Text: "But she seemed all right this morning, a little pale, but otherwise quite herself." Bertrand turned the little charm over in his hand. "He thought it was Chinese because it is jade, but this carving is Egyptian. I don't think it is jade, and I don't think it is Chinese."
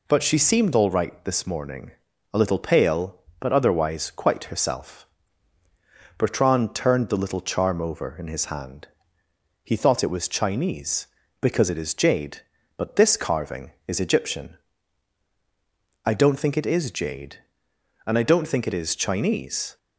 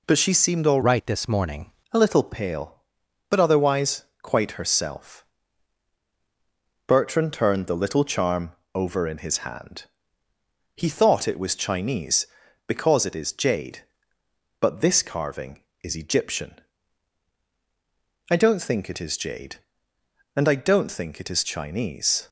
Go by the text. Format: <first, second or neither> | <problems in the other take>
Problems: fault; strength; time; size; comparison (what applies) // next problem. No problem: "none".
first | changes voice from "right" to "morning"; from 0.8 to 1.6 s; 0.8 s long // pauses between "otherwise" and "quite"; slight; at 4.0 s; 0.18 s long // pauses between "charm" and "over"; slight; at 8.5 s; 0.22 s long